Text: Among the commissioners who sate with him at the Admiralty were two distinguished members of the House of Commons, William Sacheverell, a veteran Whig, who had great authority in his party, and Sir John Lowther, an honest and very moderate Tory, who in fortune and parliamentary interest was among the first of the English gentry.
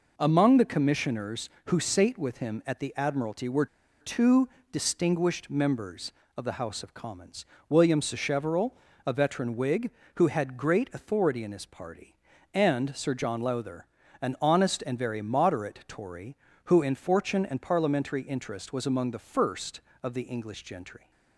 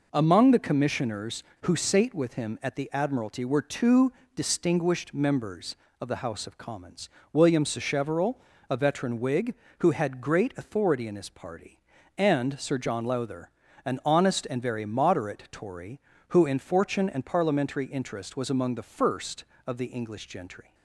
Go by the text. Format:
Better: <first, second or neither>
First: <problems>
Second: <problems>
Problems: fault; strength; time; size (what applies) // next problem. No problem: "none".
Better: second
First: pauses between "were" and "two"; slight; at 3.6 s; 0.35 s long // pauses between "two" and "distinguished"; slight; at 4.4 s; 0.24 s long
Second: pauses between "two" and "distinguished"; slight; at 4.1 s; 0.24 s long